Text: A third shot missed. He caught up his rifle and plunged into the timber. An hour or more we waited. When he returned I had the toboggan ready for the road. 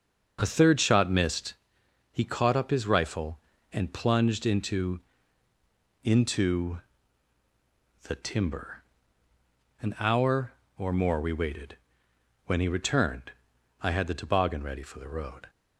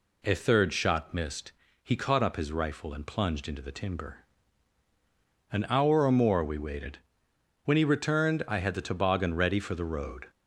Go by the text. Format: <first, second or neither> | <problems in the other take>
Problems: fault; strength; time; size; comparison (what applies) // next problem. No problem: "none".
second | starts louder than the rest; until 1.4 s; 6.5 dB // says "into" twice; at 6.0 s // pauses between "returned" and "I"; noticeable; at 13.3 s; 0.50 s long